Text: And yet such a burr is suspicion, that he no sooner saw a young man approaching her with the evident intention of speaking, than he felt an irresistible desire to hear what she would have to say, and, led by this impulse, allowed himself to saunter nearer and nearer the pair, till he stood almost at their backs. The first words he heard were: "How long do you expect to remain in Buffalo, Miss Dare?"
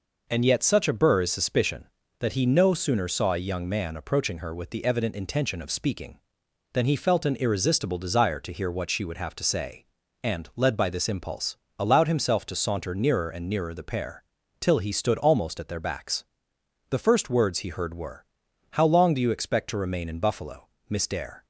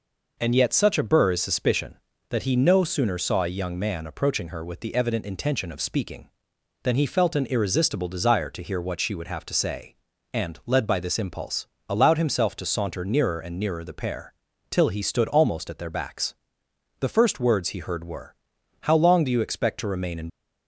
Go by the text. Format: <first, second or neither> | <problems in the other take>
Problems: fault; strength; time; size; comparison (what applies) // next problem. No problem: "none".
first | stops before "Buffalo Miss Dare"; at 20.2 s